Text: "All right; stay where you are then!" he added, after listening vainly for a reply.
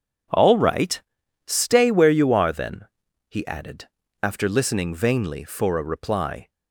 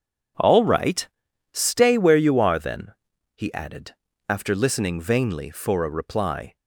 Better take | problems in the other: neither | none

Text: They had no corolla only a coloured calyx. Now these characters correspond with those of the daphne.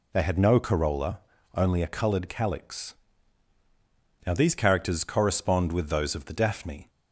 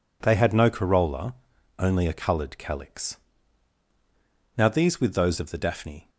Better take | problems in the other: first | pauses between "corolla" and "only"; noticeable; at 1.3 s; 0.46 s long; slight in the first // skips "characters correspond"; at 5.0 s

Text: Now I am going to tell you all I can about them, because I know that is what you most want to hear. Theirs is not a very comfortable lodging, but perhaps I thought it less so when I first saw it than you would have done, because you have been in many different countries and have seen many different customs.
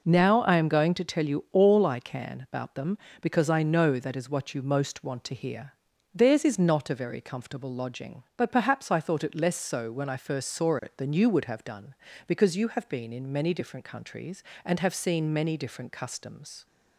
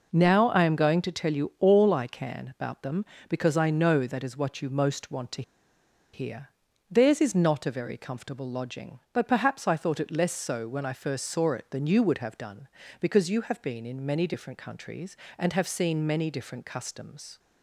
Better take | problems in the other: first | pauses between "to" and "hear"; noticeable; at 5.4 s; 0.71 s long

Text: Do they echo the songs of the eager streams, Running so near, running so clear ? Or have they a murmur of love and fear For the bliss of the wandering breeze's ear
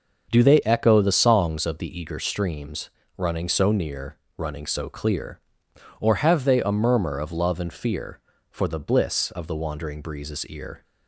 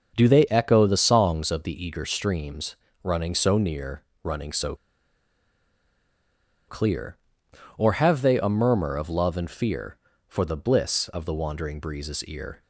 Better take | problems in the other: first | starts louder than the rest; until 1.1 s; 6.5 dB; also in the first // pauses between "so" and "clear"; strong; at 4.7 s; 1.9 s long

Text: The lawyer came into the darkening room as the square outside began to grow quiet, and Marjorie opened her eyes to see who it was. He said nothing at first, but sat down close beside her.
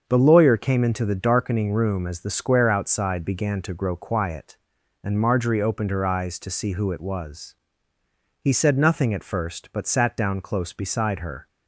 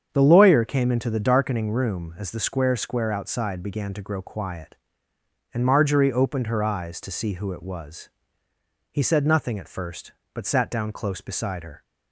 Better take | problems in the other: first | starts louder than the rest; strong; until 1.1 s; 7.5 dB; also in the first // says "square" twice; at 2.7 s

